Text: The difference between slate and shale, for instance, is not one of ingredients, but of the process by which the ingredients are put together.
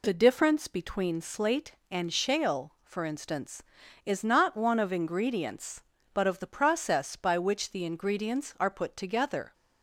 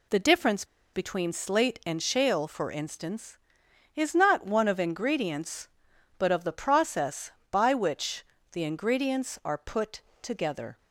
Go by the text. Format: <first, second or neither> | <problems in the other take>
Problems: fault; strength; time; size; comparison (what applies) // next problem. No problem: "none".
first | pauses between "difference" and "between"; slight; at 0.6 s; 0.28 s long // pauses between "which" and "the"; slight; at 8.2 s; 0.26 s long // pauses between "put" and "together"; slight; at 10.0 s; 0.20 s long